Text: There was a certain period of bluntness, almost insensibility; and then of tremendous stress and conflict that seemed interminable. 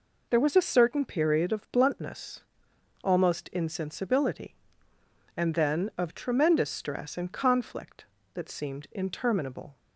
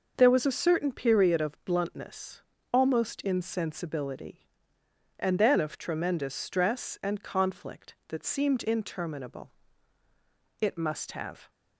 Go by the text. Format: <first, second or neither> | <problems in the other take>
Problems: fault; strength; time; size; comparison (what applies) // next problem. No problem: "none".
first | goes on to say "It must have"; noticeable; from 10.5 s on; 0.92 s long